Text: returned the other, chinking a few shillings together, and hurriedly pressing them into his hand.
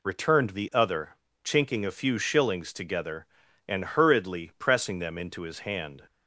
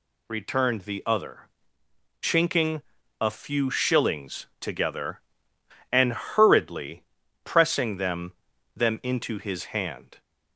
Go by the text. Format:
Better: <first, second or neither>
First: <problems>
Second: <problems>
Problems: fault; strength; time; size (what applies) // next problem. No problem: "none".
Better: first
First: none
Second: pauses between "chinking" and "a"; at 2.8 s; 0.38 s long // pauses between "hurriedly" and "pressing"; at 7.0 s; 0.40 s long // says "them" twice; at 8.7 s